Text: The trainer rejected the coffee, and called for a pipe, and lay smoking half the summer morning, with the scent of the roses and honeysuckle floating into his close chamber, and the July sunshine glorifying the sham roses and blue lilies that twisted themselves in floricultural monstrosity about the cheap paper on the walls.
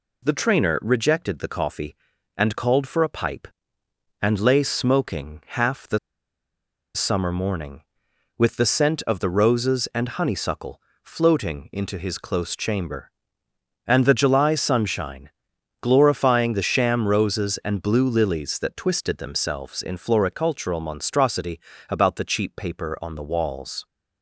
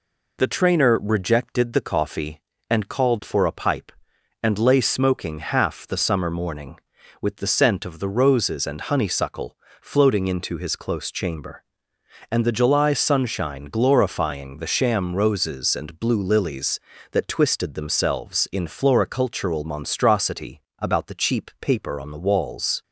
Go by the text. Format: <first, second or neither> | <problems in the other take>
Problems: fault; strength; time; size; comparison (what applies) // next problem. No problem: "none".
second | pauses between "the" and "summer"; noticeable; at 5.9 s; 0.97 s long // pauses between "honeysuckle" and "floating"; slight; at 10.7 s; 0.24 s long; slight in the second // pauses between "sunshine" and "glorifying"; noticeable; at 15.2 s; 0.54 s long // pauses between "monstrosity" and "about"; slight; at 21.5 s; 0.30 s long; slight in the second